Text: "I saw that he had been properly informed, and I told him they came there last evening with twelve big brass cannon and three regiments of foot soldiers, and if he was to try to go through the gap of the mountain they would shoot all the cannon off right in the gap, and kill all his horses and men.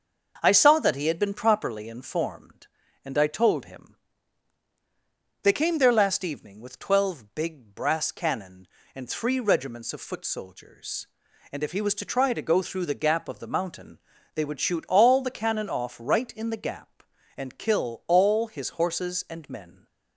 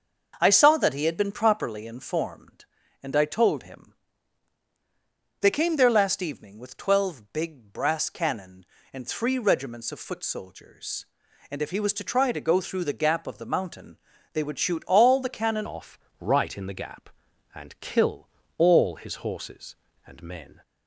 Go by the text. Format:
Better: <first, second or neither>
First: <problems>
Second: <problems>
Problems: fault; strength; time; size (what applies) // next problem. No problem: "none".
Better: first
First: starts louder than the rest; until 1.4 s; 6 dB // pauses between "him" and "they"; strong; at 3.9 s; 1.4 s long // pauses between "mountain" and "they"; slight; at 13.9 s; 0.36 s long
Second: starts louder than the rest; until 1.4 s; 6 dB // pauses between "him" and "they"; strong; at 3.9 s; 1.4 s long // pauses between "mountain" and "they"; slight; at 13.9 s; 0.36 s long // changes voice at "off"; from 15.6 s on; 5.0 s long // pauses between "off" and "right"; slight; at 15.9 s; 0.20 s long // pauses between "kill" and "all"; slight; at 18.2 s; 0.30 s long